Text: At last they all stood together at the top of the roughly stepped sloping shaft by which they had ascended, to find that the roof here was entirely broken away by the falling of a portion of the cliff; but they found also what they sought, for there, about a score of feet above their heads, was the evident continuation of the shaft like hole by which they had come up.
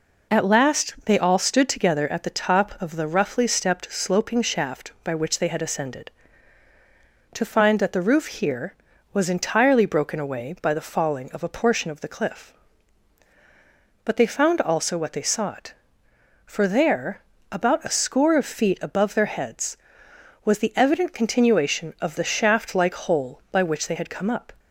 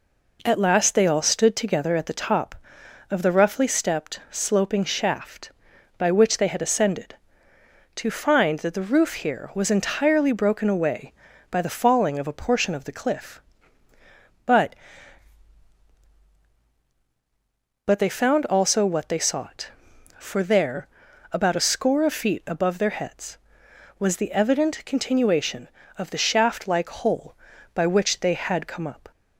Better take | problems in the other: first | says "but" twice; at 17.8 s

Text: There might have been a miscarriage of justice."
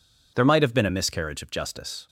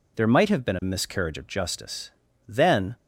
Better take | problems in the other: first | goes on to say "Then"; slight; from 2.4 s on; 0.48 s long

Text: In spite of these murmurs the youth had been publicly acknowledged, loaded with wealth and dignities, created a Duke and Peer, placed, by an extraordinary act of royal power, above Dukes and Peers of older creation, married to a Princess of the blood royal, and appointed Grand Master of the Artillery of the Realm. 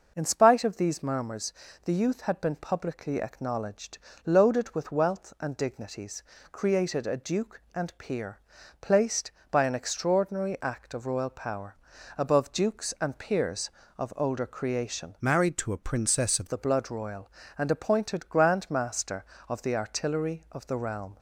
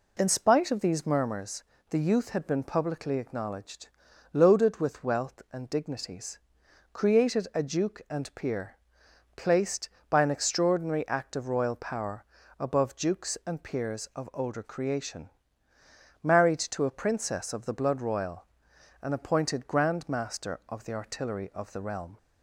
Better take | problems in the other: second | pauses between "murmurs" and "the"; slight; at 1.5 s; 0.30 s long; slight in the second // changes voice from "married" to "of"; from 15.2 to 16.4 s; 1.2 s long

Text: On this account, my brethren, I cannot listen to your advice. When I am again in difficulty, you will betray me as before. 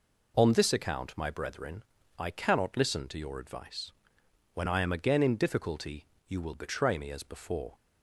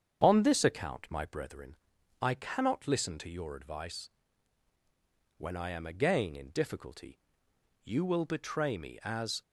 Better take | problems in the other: first | starts louder than the rest; strong; until 1.2 s; 7.5 dB // stops before "before"; at 9.4 s

